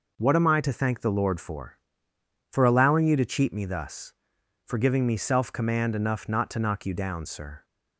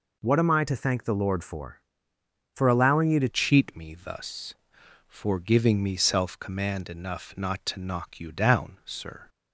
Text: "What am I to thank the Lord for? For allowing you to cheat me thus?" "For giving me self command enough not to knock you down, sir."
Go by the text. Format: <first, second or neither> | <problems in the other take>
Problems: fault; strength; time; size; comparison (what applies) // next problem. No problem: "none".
first | changes voice at "cheat"; from 3.2 s on; 6.0 s long